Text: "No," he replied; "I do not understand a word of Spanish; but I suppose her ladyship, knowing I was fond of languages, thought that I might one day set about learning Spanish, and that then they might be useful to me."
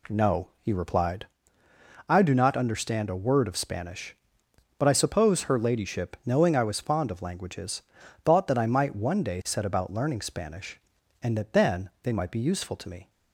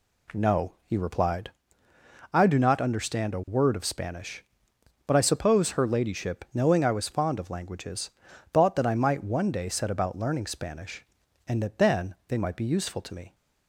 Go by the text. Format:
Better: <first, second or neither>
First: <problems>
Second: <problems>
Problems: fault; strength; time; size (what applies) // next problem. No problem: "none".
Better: neither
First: none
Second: none